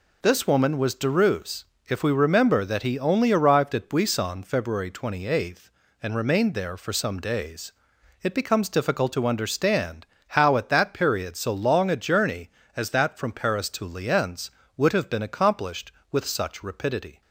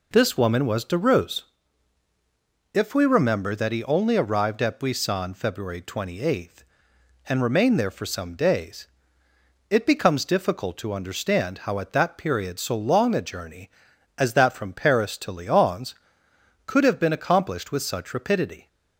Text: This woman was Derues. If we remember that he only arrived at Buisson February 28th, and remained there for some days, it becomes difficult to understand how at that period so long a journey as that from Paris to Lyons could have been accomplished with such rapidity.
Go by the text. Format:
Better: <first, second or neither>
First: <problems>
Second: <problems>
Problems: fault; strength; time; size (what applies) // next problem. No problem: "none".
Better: second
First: pauses between "understand" and "how"; slight; at 10.0 s; 0.24 s long // says "would" for "could"; at 14.7 s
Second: none